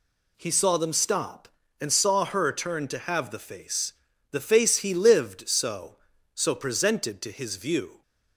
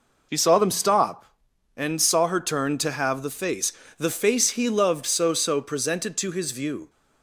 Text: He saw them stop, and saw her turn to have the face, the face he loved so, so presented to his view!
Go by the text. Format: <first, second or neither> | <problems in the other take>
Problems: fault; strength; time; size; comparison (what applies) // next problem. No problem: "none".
second | says "lived" for "loved"; at 4.9 s